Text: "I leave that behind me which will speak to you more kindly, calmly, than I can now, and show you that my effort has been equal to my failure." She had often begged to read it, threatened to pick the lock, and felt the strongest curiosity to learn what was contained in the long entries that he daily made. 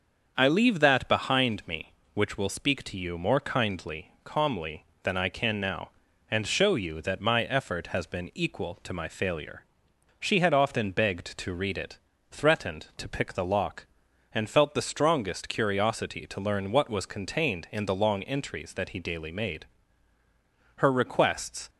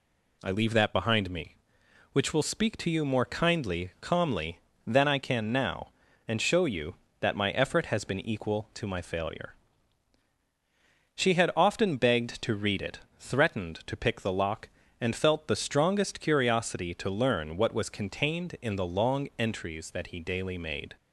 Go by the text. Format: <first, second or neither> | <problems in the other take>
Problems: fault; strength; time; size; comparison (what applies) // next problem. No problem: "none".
second | starts louder than the rest; until 1.3 s; 6.5 dB // goes on to say "Her requests"; noticeable; from 20.7 s on; 0.92 s long